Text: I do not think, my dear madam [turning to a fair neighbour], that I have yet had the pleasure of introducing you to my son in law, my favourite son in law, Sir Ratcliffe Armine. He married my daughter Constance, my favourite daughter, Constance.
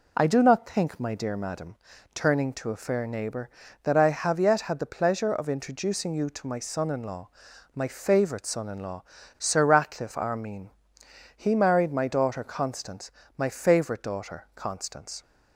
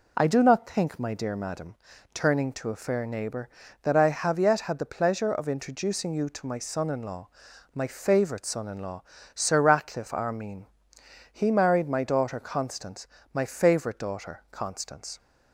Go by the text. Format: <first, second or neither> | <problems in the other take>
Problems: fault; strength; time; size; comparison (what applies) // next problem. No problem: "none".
neither | pauses between "madam" and "turning"; the same in both